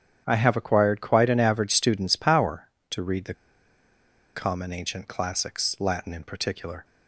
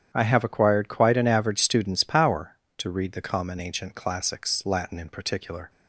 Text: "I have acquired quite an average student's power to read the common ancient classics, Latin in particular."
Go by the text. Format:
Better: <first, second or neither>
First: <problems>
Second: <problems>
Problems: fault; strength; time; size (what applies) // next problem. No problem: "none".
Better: second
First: starts louder than the rest; strong; until 1.2 s; 9 dB // pauses between "the" and "common"; at 3.3 s; 1.0 s long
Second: starts louder than the rest; strong; until 1.1 s; 9 dB